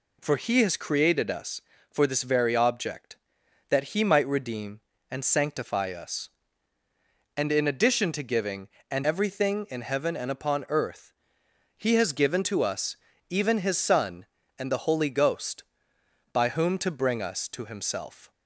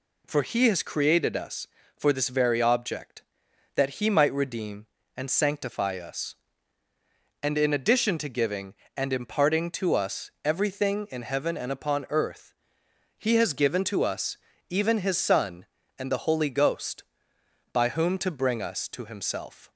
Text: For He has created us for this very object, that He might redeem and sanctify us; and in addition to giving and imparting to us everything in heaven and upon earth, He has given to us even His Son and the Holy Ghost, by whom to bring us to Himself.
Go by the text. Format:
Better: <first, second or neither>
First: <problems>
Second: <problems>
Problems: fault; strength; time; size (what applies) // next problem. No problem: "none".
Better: second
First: skips "imparting to us"; at 9.0 s // pauses between "us" and "even"; slight; at 12.9 s; 0.36 s long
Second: pauses between "us" and "even"; slight; at 14.3 s; 0.35 s long